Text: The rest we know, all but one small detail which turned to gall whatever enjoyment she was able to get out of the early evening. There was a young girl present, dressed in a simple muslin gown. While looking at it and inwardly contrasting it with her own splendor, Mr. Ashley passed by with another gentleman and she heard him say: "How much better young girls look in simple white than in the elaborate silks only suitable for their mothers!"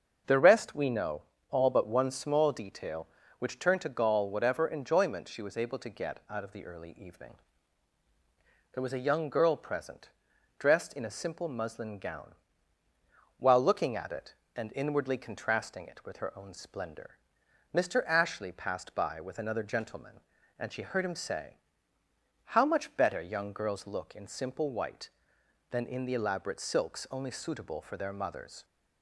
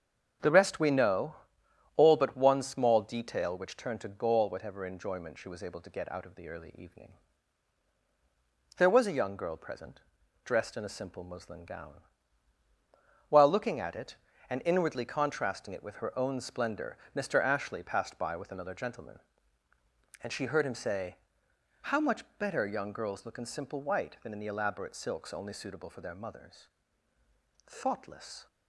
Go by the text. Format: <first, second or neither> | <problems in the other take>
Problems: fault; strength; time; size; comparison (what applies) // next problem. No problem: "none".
first | starts louder than the rest; strong; until 2.0 s; 7.5 dB; also in the first // goes on to say "Thoughtless"; noticeable; from 27.6 s on; 0.80 s long